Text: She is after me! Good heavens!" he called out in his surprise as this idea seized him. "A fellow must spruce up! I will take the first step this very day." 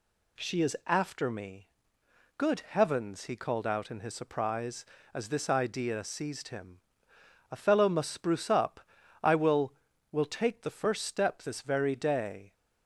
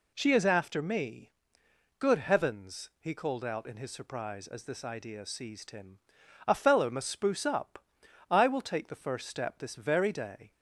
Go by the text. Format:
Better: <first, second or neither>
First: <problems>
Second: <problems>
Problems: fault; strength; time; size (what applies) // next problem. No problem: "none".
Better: second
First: says "will" twice; at 10.1 s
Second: none